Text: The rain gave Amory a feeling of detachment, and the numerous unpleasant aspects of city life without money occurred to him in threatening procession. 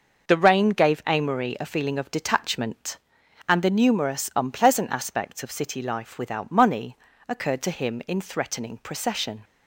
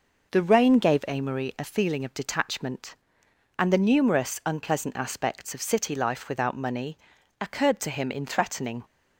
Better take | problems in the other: first | pauses between "money" and "occurred"; at 6.9 s; 0.42 s long; slight in the first // stops before "procession"; at 8.8 s

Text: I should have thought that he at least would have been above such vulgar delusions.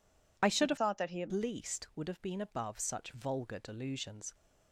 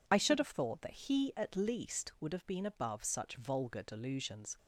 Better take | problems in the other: second | changes voice from "thought" to "at"; from 0.7 to 1.3 s; 0.6 s long

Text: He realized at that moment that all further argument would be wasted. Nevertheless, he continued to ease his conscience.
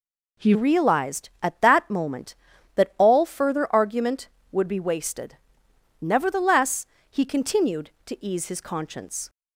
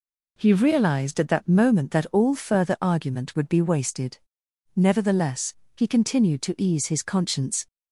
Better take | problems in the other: second | changes voice at "realized"; from 0.5 s on; 8.7 s long

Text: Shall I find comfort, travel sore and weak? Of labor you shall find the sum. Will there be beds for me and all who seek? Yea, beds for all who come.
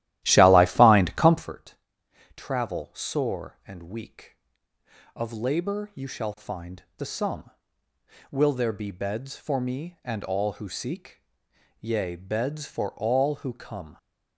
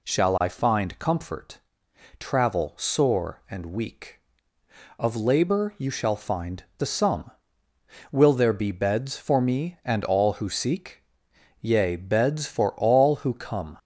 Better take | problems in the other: second | starts louder than the rest; strong; until 1.6 s; 14 dB

